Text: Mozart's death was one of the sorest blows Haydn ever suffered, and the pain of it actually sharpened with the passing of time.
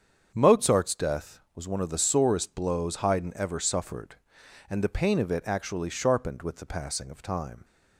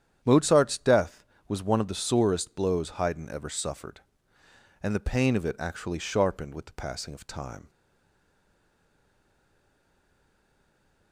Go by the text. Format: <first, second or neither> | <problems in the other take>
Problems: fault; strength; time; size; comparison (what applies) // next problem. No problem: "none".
first | starts louder than the rest; strong; until 1.2 s; 9 dB; strong in the first // stays silent after the last word; strong; from 7.6 s on; 3.5 s long